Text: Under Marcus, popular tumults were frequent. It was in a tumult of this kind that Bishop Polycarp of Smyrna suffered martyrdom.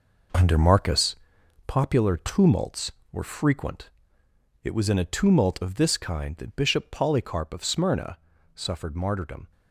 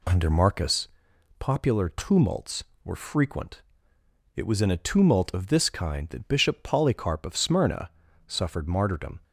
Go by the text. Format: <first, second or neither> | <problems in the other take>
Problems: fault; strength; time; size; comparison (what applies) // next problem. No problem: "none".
second | gets quieter; strong; throughout; 9 dB // pauses between "Smyrna" and "suffered"; slight; at 8.1 s; 0.36 s long; slight in the second